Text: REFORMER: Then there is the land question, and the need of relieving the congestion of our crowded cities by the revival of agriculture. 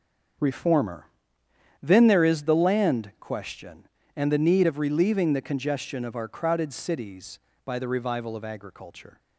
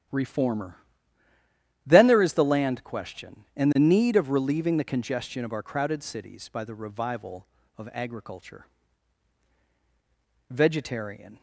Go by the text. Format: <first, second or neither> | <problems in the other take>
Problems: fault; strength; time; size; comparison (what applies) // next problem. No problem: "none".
first | starts louder than the rest; strong; until 2.1 s; 10.5 dB; also in the first // goes on to say "VEGETARIAN"; noticeable; from 10.5 s on; 0.90 s long